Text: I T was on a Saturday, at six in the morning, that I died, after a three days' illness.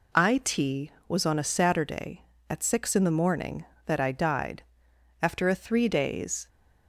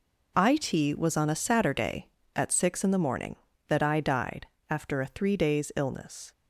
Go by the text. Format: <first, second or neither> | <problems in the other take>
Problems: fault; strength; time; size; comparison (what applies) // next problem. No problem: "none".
second | stops before "illness"; at 6.4 s